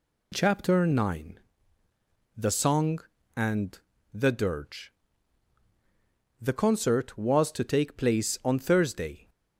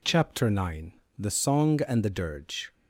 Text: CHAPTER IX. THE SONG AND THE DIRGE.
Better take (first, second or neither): second